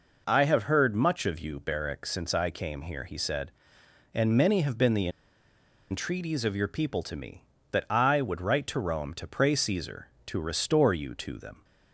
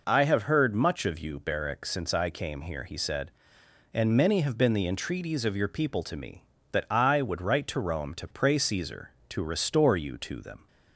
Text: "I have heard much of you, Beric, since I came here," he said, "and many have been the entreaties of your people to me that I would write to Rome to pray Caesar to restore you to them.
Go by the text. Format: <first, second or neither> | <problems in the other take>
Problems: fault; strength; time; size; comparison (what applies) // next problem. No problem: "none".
second | pauses between "the" and "entreaties"; noticeable; at 5.0 s; 0.81 s long